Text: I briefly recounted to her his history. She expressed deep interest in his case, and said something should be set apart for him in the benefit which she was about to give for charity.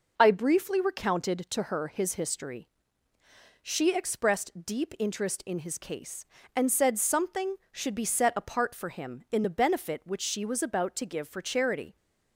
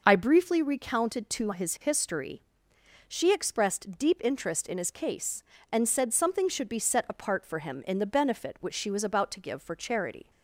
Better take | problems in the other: first | skips "her"; at 1.5 s

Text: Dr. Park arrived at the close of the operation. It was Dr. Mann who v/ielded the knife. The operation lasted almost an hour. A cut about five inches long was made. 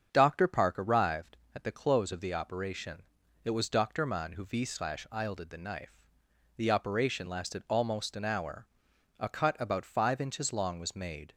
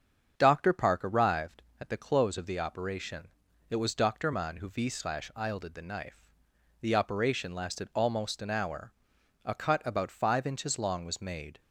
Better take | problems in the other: neither | starts louder than the rest; strong; the same in both

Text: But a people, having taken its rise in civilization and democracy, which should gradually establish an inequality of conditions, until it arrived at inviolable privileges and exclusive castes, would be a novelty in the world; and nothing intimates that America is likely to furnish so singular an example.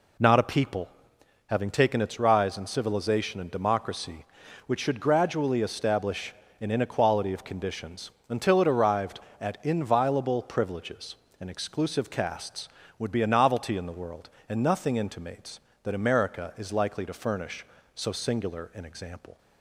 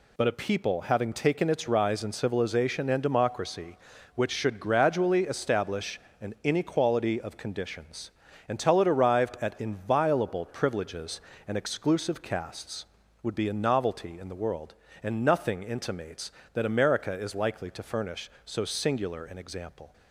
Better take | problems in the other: second | says "Not" for "But"; at 0.1 s // pauses between "establish" and "an"; slight; at 6.3 s; 0.26 s long; slight in the second

